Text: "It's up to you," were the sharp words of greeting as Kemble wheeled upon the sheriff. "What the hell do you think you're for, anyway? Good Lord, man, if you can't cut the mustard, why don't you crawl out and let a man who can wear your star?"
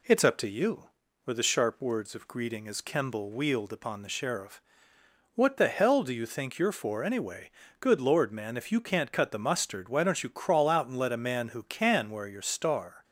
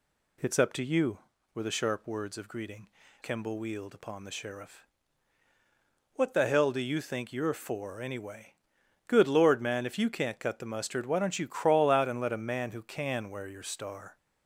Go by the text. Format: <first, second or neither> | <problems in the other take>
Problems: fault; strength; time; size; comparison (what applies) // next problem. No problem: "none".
first | skips "as"; at 3.0 s